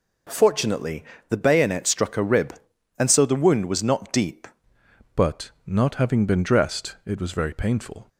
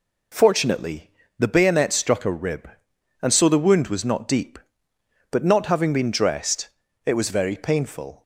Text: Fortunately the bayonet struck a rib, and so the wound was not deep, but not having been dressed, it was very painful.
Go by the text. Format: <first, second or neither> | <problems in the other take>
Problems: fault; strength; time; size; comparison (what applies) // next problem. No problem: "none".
second | pauses between "Fortunately" and "the"; slight; at 1.0 s; 0.26 s long; slight in the second // changes voice at "but"; from 5.1 s on; 2.9 s long